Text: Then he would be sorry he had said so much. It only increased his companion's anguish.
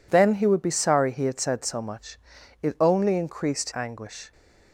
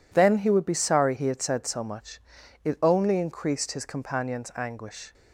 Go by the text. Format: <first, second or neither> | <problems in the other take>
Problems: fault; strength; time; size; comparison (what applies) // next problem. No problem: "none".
second | skips "his companion's"; at 3.7 s